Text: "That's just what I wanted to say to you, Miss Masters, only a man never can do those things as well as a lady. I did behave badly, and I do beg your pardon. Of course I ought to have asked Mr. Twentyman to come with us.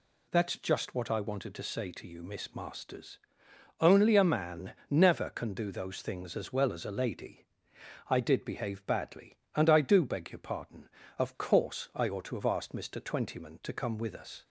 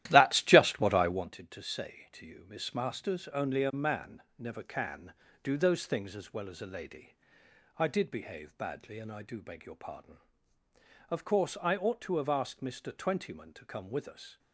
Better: first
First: pauses between "man" and "never"; slight; at 4.7 s; 0.16 s long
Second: starts louder than the rest; strong; until 1.3 s; 13.5 dB // pauses between "man" and "never"; slight; at 4.2 s; 0.16 s long

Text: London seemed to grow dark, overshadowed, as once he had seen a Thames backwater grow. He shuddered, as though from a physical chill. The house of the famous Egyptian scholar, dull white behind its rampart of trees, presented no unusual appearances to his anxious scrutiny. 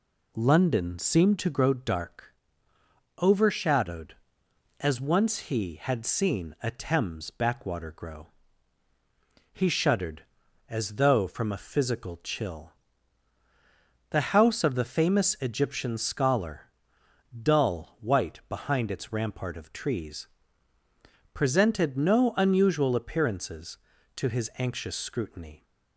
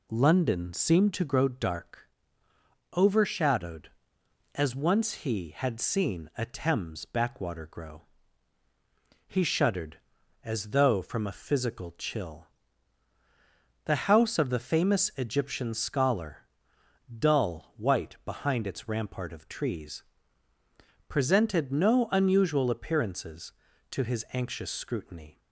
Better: neither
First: none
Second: none

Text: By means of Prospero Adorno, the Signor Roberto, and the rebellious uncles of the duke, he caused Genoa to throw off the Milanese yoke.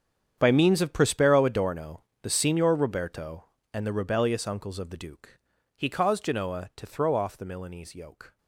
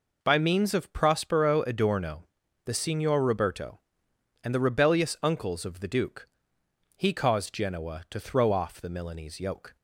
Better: second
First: gets quieter; strong; throughout; 16.5 dB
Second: none

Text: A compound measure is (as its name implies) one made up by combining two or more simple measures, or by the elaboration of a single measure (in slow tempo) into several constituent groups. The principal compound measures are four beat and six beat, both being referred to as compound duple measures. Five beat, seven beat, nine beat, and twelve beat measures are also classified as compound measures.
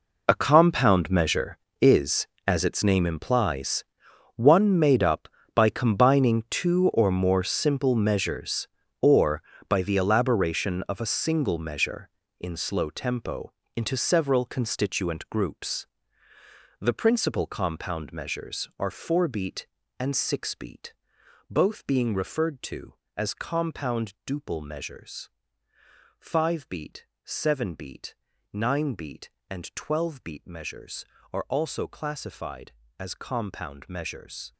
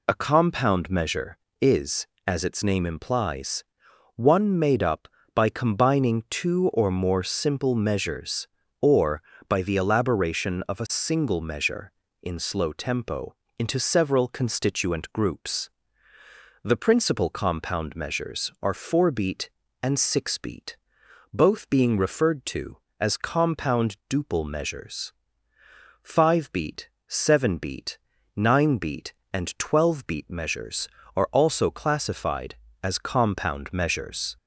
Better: second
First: gets quieter; strong; throughout; 15.5 dB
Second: none

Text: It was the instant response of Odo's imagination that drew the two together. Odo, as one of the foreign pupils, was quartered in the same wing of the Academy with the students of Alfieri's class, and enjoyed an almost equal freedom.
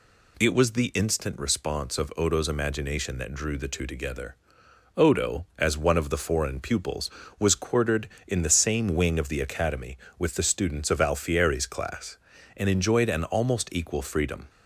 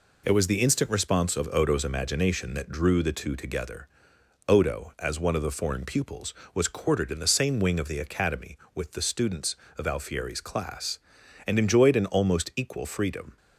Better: neither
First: none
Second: none

